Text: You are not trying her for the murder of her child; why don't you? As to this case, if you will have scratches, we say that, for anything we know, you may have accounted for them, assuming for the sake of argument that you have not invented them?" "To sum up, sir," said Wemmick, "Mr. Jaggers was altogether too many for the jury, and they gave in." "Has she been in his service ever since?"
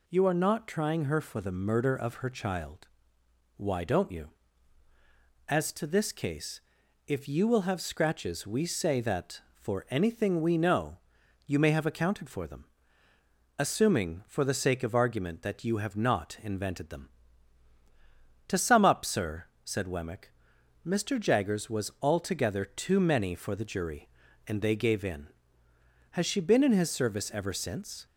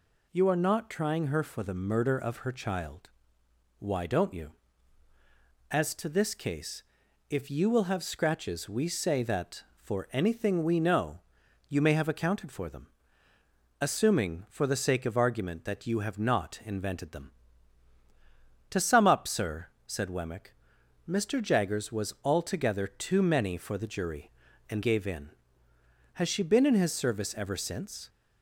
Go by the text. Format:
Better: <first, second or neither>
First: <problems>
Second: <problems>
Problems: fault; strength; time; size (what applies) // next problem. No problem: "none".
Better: first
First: none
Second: skips "they"; at 24.8 s